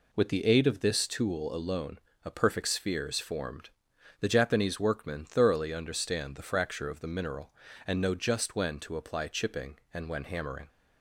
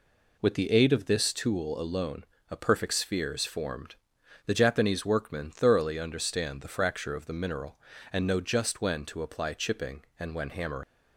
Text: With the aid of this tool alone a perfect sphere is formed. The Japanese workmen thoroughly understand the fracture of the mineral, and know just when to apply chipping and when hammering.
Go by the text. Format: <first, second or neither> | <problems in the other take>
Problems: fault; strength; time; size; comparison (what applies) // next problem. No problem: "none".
first | pauses between "alone" and "a"; slight; at 2.2 s; 0.26 s long; slight in the first // leaves "hammering" unfinished; at 10.8 s; 100 ms